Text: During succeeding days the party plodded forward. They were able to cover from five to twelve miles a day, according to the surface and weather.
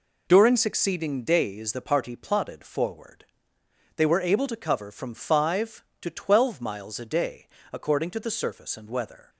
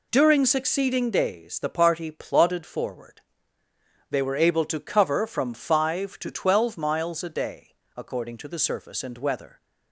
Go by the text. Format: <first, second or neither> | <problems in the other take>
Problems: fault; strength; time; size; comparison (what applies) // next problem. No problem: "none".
neither | none